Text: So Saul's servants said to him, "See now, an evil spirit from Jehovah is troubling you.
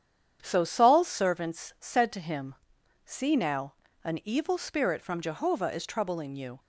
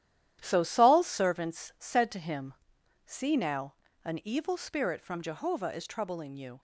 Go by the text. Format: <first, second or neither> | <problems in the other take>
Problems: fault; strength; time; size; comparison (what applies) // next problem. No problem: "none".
first | gets quieter; strong; throughout; 8 dB // starts louder than the rest; strong; until 1.4 s; 11.5 dB; strong in the first